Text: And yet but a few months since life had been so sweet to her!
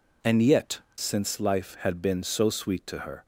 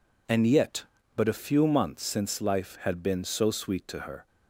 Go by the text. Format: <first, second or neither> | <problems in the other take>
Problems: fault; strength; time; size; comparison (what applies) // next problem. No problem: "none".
second | skips "but a few months"; at 0.9 s